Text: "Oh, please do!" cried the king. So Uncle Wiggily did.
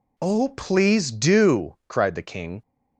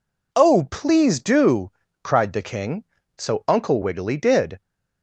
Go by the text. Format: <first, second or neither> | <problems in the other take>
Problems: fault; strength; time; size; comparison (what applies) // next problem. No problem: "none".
second | stops before "So Uncle Wiggily did"; at 2.6 s